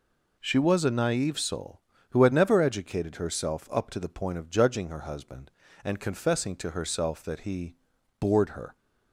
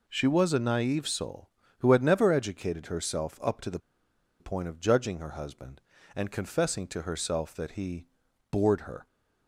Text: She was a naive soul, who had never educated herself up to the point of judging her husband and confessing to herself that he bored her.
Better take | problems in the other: first | pauses between "the" and "point"; noticeable; at 3.7 s; 0.61 s long // pauses between "he" and "bored"; at 8.0 s; 0.44 s long; also in the first

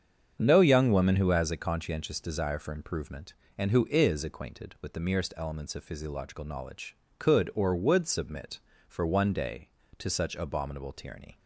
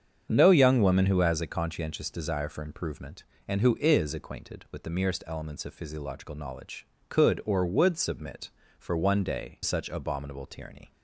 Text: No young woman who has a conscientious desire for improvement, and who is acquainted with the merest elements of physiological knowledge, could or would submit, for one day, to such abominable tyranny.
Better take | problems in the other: first | starts louder than the rest; strong; until 1.3 s; 7 dB; strong in the first // skips "to"; at 9.6 s

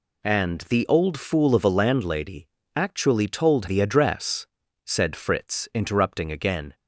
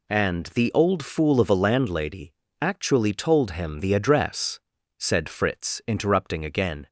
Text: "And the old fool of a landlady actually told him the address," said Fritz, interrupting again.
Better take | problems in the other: second | pauses between "landlady" and "actually"; slight; at 2.4 s; 0.30 s long; slight in the second // skips "him"; at 3.6 s

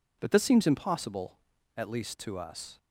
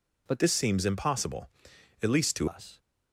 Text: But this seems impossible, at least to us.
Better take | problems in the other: first | changes voice from "this" to "to"; from 0.3 to 2.4 s; 2.1 s long

